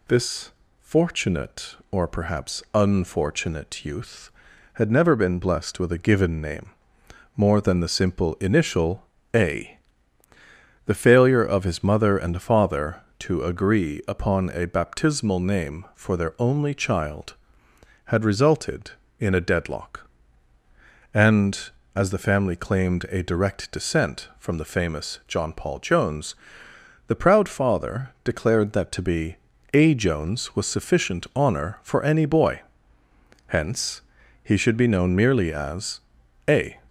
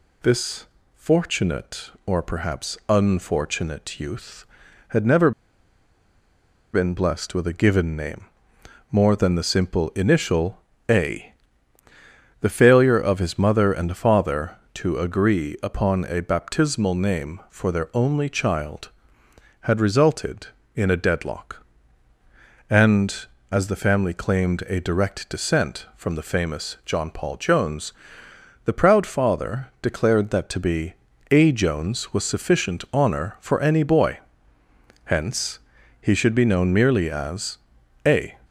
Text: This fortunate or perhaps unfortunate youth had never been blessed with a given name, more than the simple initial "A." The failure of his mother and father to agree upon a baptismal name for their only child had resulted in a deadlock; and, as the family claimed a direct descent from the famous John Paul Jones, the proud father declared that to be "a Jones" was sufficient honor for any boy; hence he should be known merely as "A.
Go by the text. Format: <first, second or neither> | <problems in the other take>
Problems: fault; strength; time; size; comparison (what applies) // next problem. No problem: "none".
first | pauses between "This" and "fortunate"; slight; at 0.6 s; 0.28 s long; slight in the first // pauses between "never" and "been"; strong; at 5.3 s; 1.4 s long // pauses between "initial" and "A"; slight; at 10.6 s; 0.30 s long; slight in the first // pauses between "be" and "a"; slight; at 30.9 s; 0.36 s long; slight in the first // pauses between "hence" and "he"; at 35.5 s; 0.42 s long; also in the first // pauses between "as" and "A"; noticeable; at 37.5 s; 0.48 s long; noticeable in the first